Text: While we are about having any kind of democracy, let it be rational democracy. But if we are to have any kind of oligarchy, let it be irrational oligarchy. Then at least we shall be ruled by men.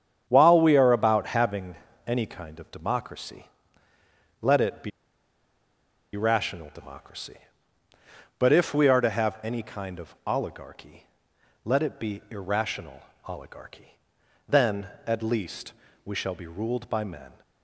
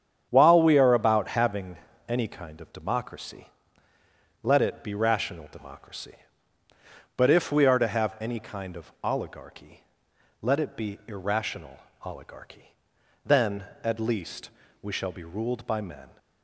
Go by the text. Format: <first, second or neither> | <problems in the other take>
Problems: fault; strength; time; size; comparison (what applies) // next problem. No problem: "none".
second | starts louder than the rest; strong; until 1.2 s; 8.5 dB; strong in the second // pauses between "having" and "any"; slight; at 1.7 s; 0.30 s long; slight in the second // pauses between "be" and "rational"; strong; at 4.9 s; 1.2 s long // pauses between "irrational" and "oligarchy"; slight; at 13.0 s; 0.24 s long; slight in the second // pauses between "least" and "we"; slight; at 15.7 s; 0.32 s long; slight in the second